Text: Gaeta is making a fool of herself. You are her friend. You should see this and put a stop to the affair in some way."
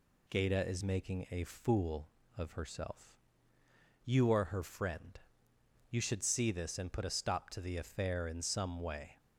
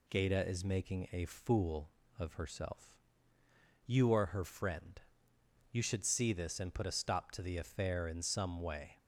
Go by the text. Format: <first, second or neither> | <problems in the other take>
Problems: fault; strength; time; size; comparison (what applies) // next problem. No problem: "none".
neither | none